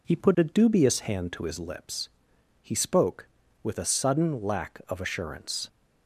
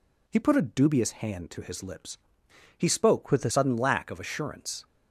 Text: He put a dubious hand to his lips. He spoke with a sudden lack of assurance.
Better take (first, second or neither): first